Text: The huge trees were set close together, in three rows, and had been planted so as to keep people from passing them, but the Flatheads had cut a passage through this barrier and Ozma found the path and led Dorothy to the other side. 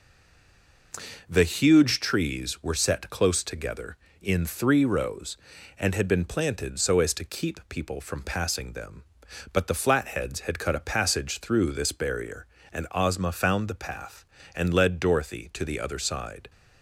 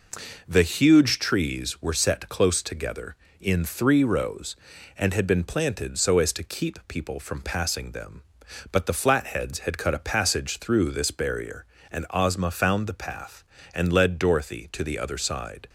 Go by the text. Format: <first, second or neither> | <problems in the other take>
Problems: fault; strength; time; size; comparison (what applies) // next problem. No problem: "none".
second | stays silent before the first word; slight; until 0.9 s; 0.9 s long